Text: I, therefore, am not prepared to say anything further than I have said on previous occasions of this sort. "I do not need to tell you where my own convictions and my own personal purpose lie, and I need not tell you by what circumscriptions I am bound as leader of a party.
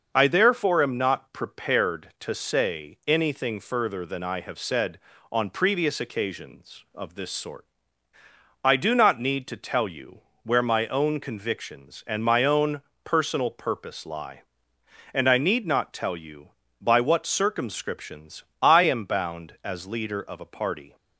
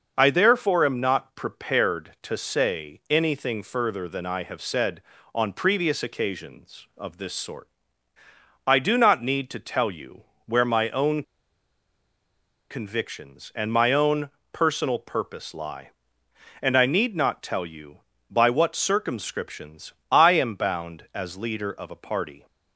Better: first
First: starts louder than the rest; until 1.1 s; 6.5 dB // pauses between "you" and "where"; slight; at 10.1 s; 0.24 s long // pauses between "own" and "personal"; slight; at 12.8 s; 0.24 s long // pauses between "circumscriptions" and "I"; slight; at 18.4 s; 0.18 s long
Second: starts louder than the rest; until 1.1 s; 6.5 dB // pauses between "you" and "where"; slight; at 10.2 s; 0.24 s long // pauses between "own" and "convictions"; strong; at 11.2 s; 1.4 s long // pauses between "own" and "personal"; slight; at 14.2 s; 0.24 s long // pauses between "circumscriptions" and "I"; slight; at 19.9 s; 0.18 s long

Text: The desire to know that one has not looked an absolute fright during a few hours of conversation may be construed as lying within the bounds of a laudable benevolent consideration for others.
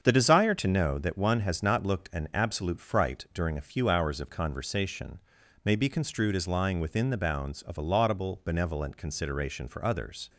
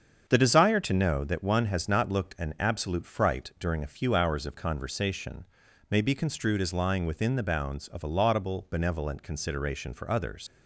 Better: first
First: starts louder than the rest; strong; until 1.0 s; 7 dB // pauses between "conversation" and "may"; noticeable; at 5.1 s; 0.46 s long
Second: starts louder than the rest; strong; until 1.2 s; 7 dB // pauses between "conversation" and "may"; noticeable; at 5.4 s; 0.46 s long // leaves "others" unfinished; at 10.4 s; 80 ms

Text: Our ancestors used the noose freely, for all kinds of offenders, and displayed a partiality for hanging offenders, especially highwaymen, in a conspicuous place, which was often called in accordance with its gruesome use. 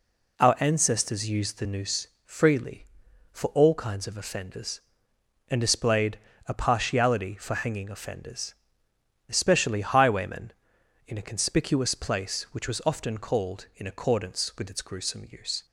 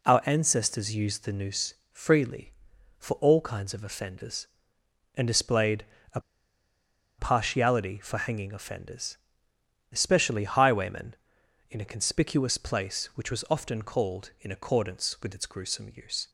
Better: first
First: pauses between "noose" and "freely"; slight; at 2.0 s; 0.16 s long // pauses between "displayed" and "a"; slight; at 6.1 s; 0.28 s long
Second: pauses between "noose" and "freely"; slight; at 1.7 s; 0.16 s long // pauses between "displayed" and "a"; slight; at 5.8 s; 0.28 s long // pauses between "a" and "partiality"; at 6.1 s; 0.99 s long

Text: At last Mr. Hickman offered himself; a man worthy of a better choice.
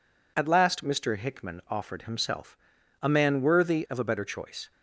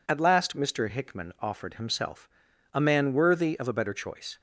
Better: neither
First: none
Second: none

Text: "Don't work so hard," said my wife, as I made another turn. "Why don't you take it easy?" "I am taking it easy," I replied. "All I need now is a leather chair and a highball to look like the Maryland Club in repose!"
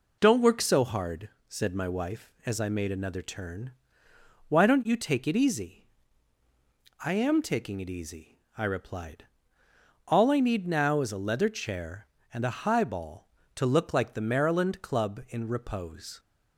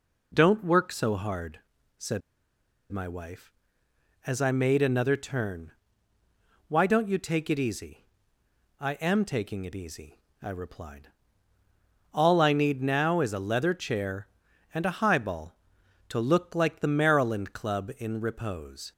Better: first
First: none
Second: pauses between "said" and "my"; noticeable; at 2.2 s; 0.71 s long

